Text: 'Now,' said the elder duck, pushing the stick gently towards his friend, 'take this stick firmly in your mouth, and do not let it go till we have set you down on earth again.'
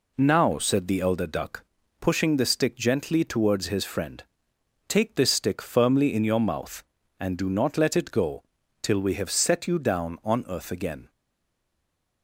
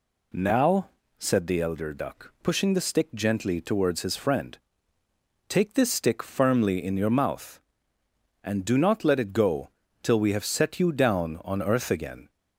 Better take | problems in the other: second | pauses between "go" and "till"; at 8.4 s; 0.40 s long; slight in the second // stays silent after the last word; from 11.0 s on; 1.2 s long

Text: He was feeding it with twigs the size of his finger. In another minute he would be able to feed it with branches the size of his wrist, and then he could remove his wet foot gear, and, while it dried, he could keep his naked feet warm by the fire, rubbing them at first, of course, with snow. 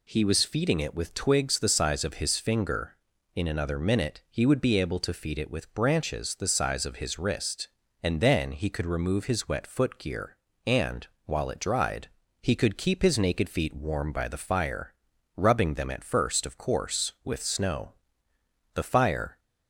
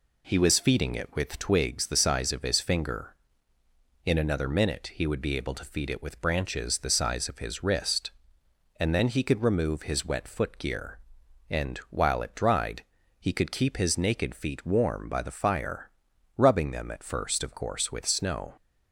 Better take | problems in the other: second | goes on to say "The fire"; noticeable; from 18.7 s on; 0.64 s long

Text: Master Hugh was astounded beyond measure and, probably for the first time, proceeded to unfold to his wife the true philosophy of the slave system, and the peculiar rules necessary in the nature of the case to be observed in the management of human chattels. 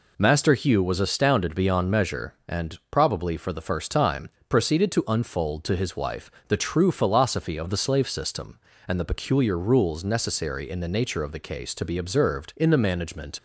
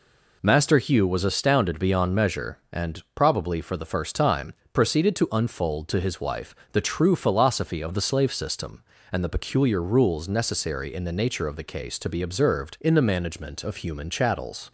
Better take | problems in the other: second | pauses between "wife" and "the"; slight; at 6.3 s; 0.16 s long; slight in the second // stops before "of human chattels"; at 13.3 s

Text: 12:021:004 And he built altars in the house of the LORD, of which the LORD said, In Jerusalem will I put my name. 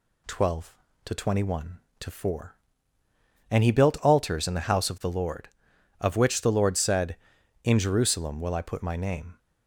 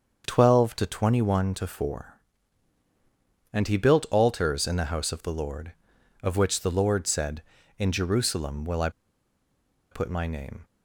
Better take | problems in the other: first | starts louder than the rest; until 1.2 s; 6.5 dB // pauses between "I" and "put"; at 8.8 s; 1.0 s long

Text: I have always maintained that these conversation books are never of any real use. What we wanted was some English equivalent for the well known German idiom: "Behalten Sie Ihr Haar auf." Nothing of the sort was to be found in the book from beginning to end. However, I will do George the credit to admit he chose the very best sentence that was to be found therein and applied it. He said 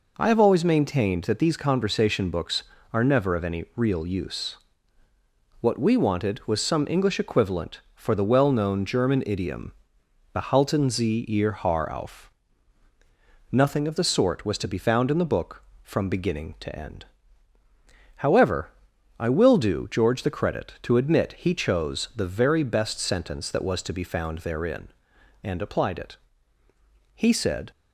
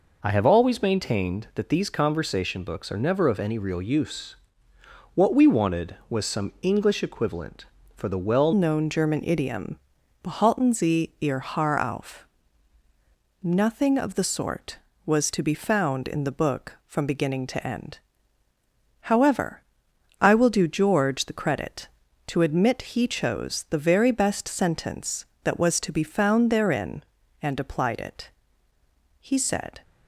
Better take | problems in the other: first | changes voice at "known"; from 8.5 s on; 21.3 s long

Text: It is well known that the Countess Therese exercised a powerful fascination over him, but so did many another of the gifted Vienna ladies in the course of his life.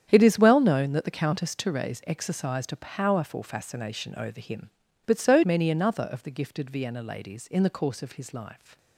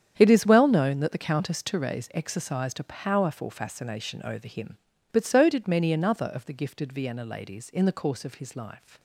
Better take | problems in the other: second | starts louder than the rest; strong; until 1.1 s; 9 dB; strong in the second // skips "did"; at 5.4 s

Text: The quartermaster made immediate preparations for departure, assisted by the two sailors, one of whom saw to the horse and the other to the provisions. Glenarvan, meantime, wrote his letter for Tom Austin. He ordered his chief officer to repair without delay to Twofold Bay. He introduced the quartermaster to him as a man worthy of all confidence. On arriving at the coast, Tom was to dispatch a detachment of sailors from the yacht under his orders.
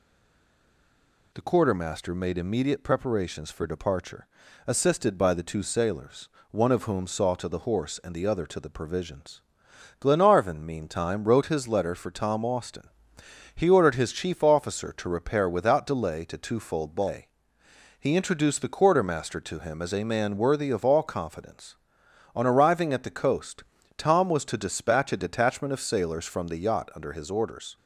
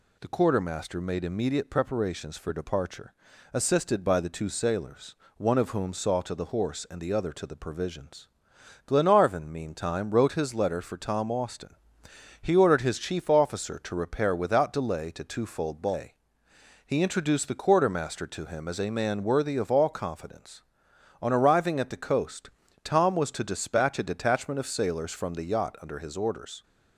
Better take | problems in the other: second | stays silent before the first word; noticeable; until 1.3 s; 1.3 s long

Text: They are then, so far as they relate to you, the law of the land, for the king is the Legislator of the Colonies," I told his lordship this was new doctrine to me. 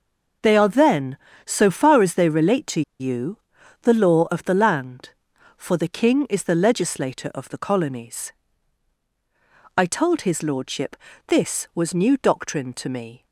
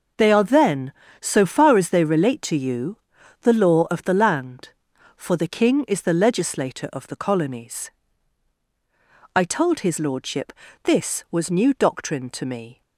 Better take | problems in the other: second | pauses between "to" and "you"; slight; at 2.8 s; 0.18 s long // pauses between "lordship" and "this"; slight; at 10.9 s; 0.30 s long; slight in the second

